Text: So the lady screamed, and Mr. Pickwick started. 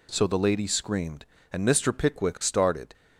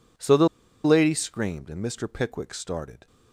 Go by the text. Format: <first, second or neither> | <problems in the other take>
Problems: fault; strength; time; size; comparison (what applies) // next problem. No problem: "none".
first | pauses between "the" and "lady"; at 0.4 s; 0.36 s long